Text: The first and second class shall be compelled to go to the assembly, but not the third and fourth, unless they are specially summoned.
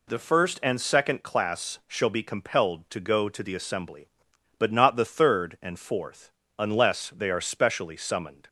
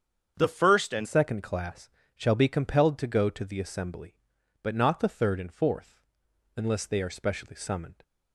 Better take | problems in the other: first | starts louder than the rest; strong; until 1.3 s; 7.5 dB // changes voice at "second"; from 1.0 s on; 7.0 s long // pauses between "class" and "shall"; slight; at 1.9 s; 0.24 s long

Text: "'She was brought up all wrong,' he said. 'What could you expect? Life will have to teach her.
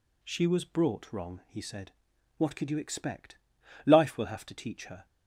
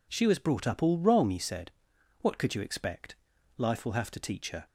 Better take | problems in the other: second | skips "up all"; at 1.1 s

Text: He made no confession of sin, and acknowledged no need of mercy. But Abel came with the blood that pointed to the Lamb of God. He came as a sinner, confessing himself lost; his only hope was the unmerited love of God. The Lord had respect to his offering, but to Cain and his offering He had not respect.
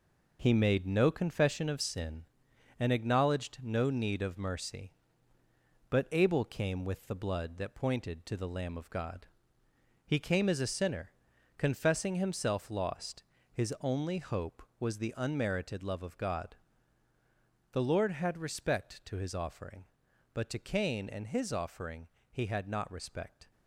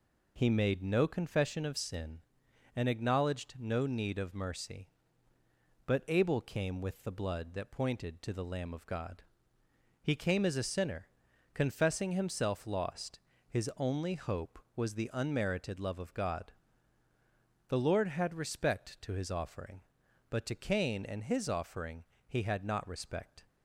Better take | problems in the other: second | gets quieter; throughout; 7 dB // pauses between "offering" and "He"; slight; at 22.0 s; 0.26 s long; slight in the second

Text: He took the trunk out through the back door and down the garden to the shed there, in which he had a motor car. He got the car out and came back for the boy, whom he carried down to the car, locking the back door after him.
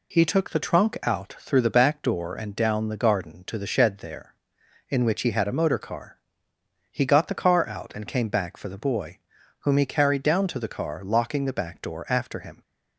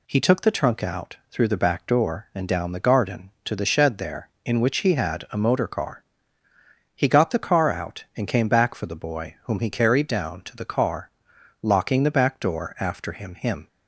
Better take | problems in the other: first | says "him" twice; at 13.3 s

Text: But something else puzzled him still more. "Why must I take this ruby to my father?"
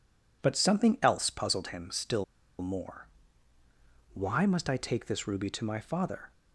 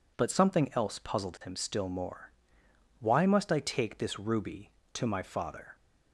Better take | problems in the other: second | pauses between "still" and "more"; at 2.2 s; 0.37 s long

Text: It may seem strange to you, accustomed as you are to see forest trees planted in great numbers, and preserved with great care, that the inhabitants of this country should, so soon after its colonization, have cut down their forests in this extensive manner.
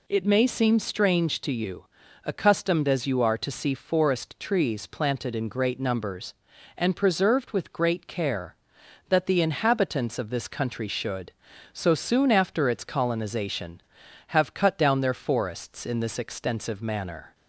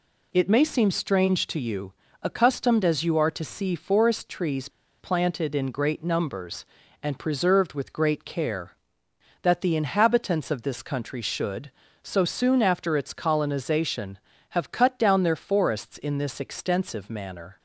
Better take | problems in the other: first | pauses between "trees" and "planted"; slight; at 4.6 s; 0.31 s long

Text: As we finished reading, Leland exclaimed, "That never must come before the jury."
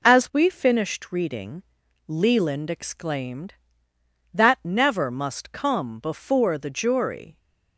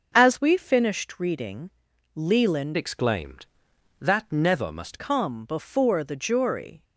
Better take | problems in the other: first | starts louder than the rest; noticeable; until 1.1 s; 6 dB // changes voice from "exclaimed" to "must"; from 2.7 to 4.9 s; 2.2 s long

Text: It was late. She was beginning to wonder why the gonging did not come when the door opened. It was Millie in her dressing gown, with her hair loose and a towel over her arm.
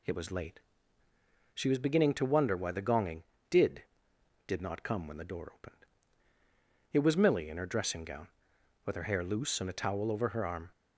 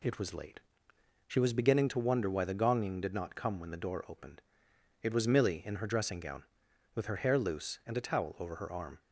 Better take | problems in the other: second | says "did" twice; at 4.4 s

